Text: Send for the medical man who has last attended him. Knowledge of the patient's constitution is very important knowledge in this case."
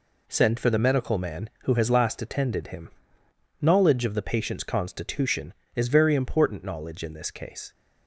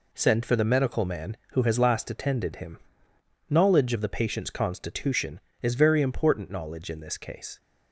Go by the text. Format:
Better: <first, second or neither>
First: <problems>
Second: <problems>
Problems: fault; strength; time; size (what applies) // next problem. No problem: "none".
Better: neither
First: none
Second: none